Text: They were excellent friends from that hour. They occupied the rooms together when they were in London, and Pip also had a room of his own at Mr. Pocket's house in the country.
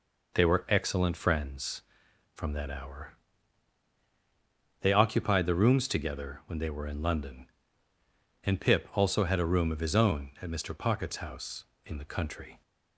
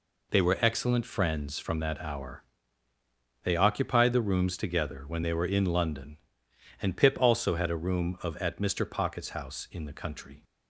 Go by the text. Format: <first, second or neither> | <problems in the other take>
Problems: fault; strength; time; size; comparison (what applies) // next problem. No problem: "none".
first | skips "his own"; at 8.3 s